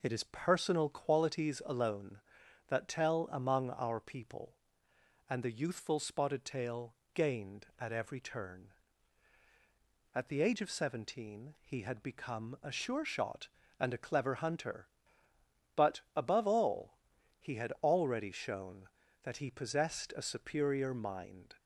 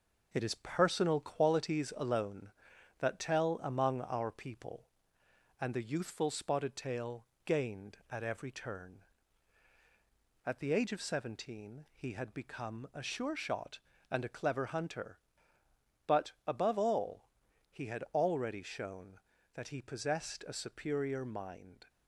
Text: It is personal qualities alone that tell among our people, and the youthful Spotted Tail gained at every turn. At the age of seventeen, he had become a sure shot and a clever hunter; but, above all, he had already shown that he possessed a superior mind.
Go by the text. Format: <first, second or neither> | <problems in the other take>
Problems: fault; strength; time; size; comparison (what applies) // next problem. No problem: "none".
first | gets quieter; noticeable; throughout; 4 dB // pauses between "Tail" and "gained"; slight; at 7.2 s; 0.20 s long; slight in the first